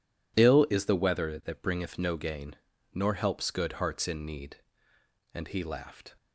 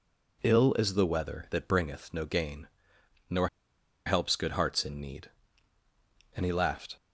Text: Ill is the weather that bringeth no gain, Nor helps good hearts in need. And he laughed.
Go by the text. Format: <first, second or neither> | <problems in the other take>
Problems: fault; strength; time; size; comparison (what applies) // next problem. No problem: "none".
first | pauses between "Nor" and "helps"; noticeable; at 3.4 s; 0.58 s long